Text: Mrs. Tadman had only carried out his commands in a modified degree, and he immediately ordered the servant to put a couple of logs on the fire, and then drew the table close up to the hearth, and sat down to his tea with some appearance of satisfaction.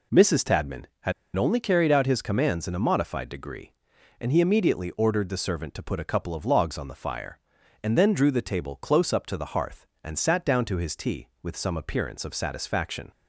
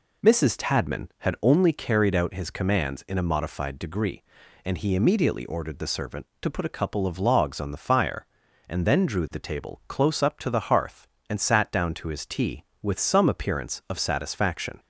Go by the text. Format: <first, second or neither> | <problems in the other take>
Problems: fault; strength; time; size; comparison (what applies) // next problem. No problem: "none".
second | pauses between "had" and "only"; slight; at 1.1 s; 0.23 s long